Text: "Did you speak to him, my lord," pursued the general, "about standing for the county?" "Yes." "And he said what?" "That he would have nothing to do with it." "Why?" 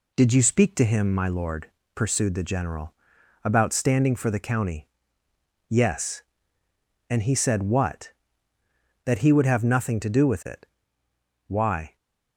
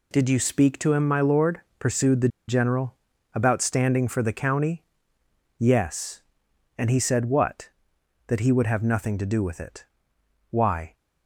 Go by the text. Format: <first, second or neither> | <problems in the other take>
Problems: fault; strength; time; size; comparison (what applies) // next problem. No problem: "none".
first | pauses between "the" and "general"; slight; at 2.2 s; 0.19 s long